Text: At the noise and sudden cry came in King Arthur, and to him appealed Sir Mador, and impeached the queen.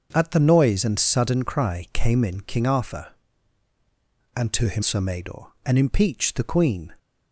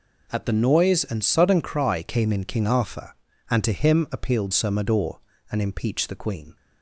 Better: second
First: starts louder than the rest; until 1.1 s; 6.5 dB // skips "appealed"; at 4.8 s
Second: none

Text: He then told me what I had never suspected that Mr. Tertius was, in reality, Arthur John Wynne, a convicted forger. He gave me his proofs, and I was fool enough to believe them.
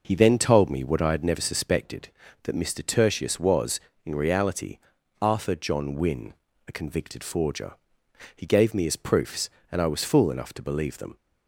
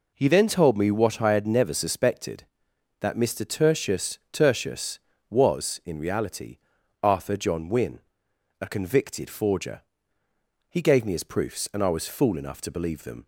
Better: first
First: none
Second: says "Tertius" twice; at 4.3 s

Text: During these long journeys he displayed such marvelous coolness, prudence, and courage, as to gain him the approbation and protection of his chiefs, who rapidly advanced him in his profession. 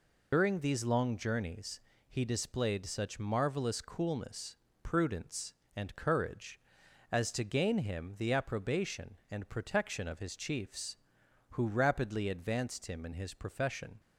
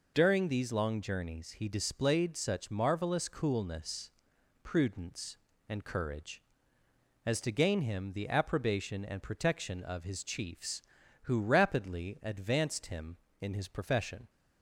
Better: second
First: loses the start of "During"; at 0.3 s; 135 ms // pauses between "journeys" and "he"; slight; at 1.7 s; 0.30 s long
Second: none

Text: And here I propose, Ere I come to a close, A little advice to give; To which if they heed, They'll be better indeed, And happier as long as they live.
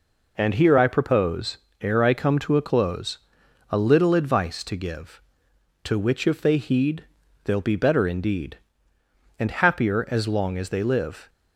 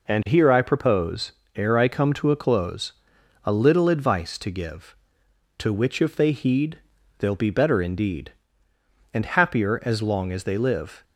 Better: neither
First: none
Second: none

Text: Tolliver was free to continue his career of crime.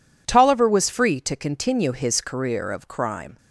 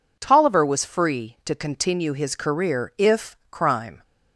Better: first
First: none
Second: says "if" for "of"; at 2.9 s

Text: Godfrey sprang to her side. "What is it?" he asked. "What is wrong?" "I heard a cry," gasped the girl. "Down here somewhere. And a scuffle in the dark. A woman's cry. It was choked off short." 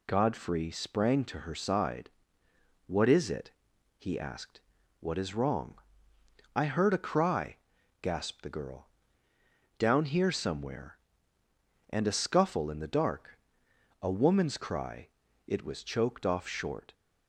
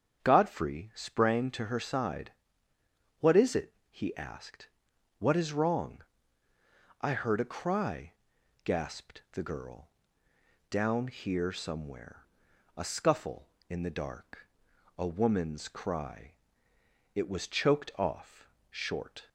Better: first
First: none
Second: starts louder than the rest; strong; until 1.2 s; 8 dB // skips "And"; at 12.5 s // pauses between "off" and "short"; slight; at 18.4 s; 0.20 s long

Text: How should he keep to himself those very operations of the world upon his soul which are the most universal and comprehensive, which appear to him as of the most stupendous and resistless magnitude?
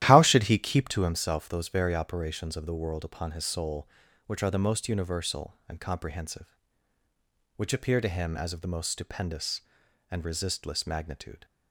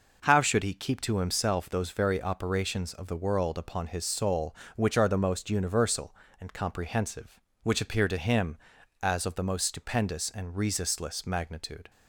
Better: second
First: starts louder than the rest; strong; until 1.1 s; 12.5 dB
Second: none

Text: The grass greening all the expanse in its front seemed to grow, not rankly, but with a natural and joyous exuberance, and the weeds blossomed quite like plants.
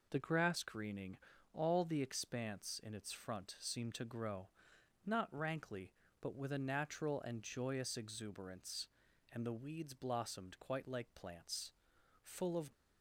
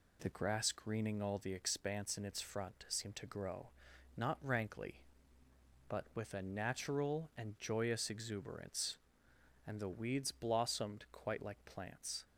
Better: second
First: pauses between "greening" and "all"; slight; at 1.1 s; 0.36 s long // goes on to say "Full of"; slight; from 12.2 s on; 0.48 s long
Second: none

